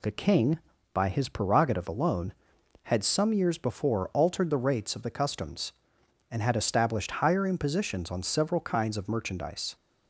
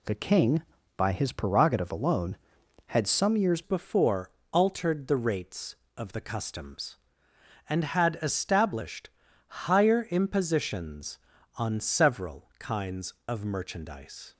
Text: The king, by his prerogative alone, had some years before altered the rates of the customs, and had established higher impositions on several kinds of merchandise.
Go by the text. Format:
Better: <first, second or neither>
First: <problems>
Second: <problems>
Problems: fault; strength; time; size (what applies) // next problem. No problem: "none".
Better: first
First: none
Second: changes voice at "before"; from 3.6 s on; 10.7 s long // pauses between "before" and "altered"; slight; at 4.3 s; 0.20 s long // pauses between "established" and "higher"; slight; at 9.1 s; 0.36 s long